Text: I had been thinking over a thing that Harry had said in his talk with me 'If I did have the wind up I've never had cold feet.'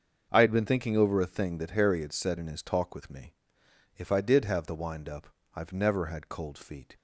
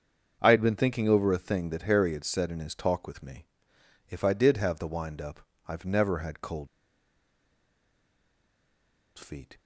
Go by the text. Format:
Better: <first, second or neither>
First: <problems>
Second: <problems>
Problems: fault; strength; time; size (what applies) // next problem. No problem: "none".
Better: first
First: starts louder than the rest; until 1.3 s; 6.5 dB // pauses between "me" and "If"; noticeable; at 3.3 s; 0.62 s long // pauses between "up" and "I've"; slight; at 5.2 s; 0.26 s long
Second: starts louder than the rest; until 1.4 s; 6.5 dB // pauses between "me" and "If"; noticeable; at 3.4 s; 0.62 s long // pauses between "up" and "I've"; slight; at 5.4 s; 0.26 s long // pauses between "cold" and "feet"; strong; at 6.6 s; 2.5 s long